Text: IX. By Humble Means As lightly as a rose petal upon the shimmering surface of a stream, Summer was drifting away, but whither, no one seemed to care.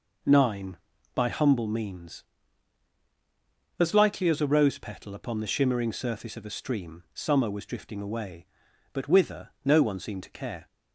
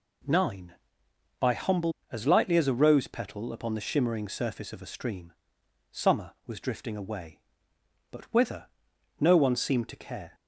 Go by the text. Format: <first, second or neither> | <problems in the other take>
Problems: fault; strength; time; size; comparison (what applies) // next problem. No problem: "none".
first | skips "Means"; at 2.0 s